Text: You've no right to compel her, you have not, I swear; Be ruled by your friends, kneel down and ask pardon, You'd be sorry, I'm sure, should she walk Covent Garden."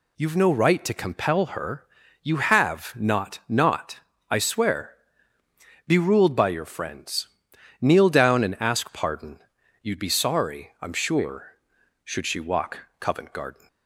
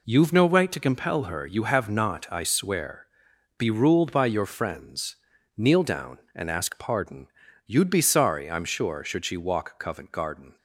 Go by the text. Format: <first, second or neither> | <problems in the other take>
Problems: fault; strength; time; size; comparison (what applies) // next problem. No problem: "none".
second | says "not" twice; at 3.4 s // pauses between "walk" and "Covent"; slight; at 12.8 s; 0.16 s long